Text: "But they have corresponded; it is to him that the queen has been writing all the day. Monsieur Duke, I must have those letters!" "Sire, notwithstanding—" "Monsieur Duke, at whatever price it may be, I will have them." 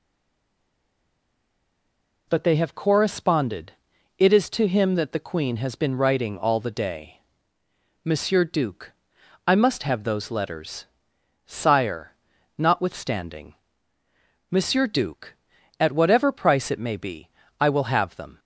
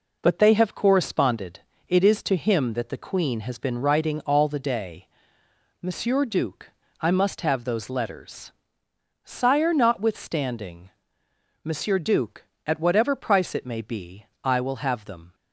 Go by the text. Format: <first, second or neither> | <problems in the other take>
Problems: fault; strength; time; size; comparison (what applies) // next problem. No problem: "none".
second | stays silent before the first word; until 2.2 s; 2.2 s long